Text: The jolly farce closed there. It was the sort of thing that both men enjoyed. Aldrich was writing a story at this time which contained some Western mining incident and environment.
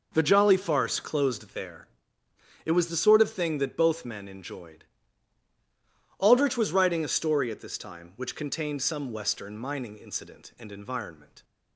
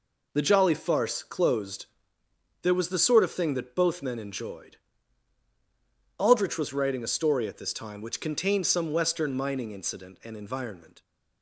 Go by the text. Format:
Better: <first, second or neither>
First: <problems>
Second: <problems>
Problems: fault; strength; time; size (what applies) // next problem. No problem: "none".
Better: first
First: none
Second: pauses between "closed" and "there"; noticeable; at 1.8 s; 0.76 s long // skips "It"; at 2.7 s